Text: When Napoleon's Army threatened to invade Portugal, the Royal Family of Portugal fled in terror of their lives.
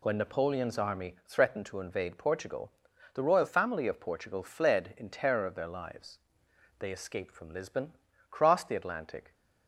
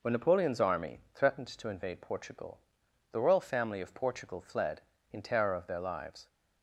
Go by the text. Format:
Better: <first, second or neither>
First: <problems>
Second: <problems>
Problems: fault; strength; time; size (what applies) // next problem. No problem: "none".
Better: second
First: goes on to say "They escaped from Lisbon crossed the Atlantic"; strong; from 6.7 s on; 2.5 s long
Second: none